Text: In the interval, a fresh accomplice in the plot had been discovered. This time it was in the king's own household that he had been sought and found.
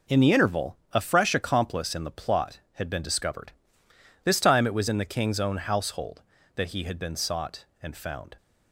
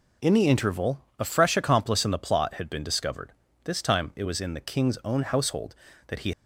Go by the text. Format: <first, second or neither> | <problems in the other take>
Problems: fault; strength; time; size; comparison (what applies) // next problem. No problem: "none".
first | stops before "had been sought and found"; at 6.3 s